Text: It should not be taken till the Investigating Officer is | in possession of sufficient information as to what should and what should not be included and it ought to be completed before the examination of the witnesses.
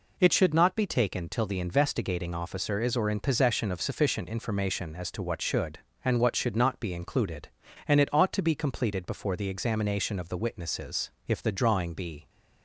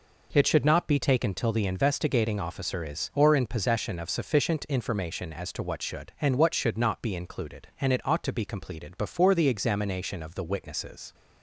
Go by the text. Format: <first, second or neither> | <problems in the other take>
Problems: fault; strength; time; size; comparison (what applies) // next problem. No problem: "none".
second | goes on to say "If the drawing be"; noticeable; from 11.2 s on; 1.0 s long